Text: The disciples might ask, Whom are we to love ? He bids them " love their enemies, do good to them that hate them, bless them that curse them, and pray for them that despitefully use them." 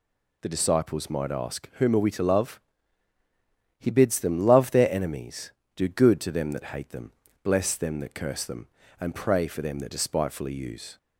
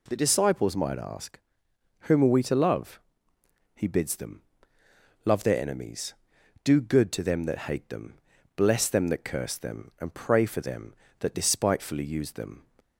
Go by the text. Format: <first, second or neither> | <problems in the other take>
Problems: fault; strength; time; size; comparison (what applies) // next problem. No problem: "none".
second | stops before "them"; at 10.9 s